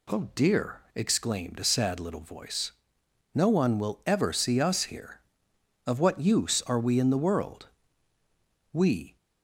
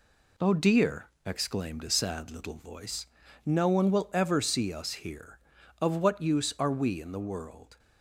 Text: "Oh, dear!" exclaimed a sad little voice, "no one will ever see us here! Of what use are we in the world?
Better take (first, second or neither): second